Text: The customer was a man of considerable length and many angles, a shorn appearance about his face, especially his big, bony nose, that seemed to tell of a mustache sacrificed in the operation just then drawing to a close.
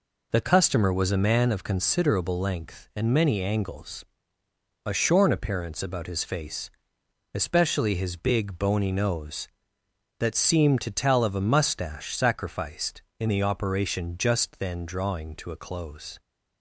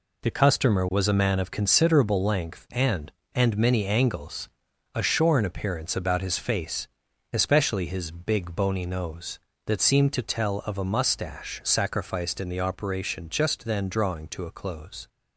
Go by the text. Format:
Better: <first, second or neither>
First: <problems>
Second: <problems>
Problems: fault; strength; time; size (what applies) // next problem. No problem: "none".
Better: first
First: none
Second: says "and" twice; at 3.3 s